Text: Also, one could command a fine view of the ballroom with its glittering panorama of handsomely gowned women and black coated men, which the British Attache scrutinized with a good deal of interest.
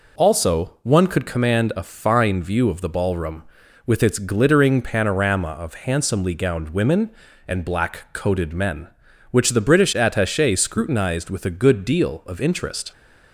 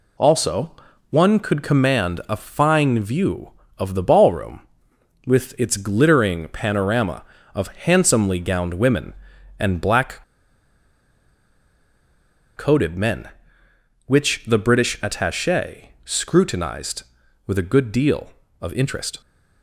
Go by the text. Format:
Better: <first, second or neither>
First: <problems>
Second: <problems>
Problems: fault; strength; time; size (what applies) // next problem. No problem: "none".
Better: first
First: none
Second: pauses between "black" and "coated"; strong; at 10.2 s; 2.3 s long